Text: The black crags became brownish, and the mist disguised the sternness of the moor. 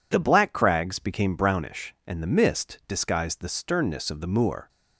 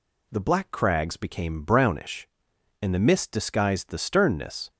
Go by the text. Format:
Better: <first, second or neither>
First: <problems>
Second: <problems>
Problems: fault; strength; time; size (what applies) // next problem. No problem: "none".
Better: first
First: none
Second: stops before "of the moor"; at 4.7 s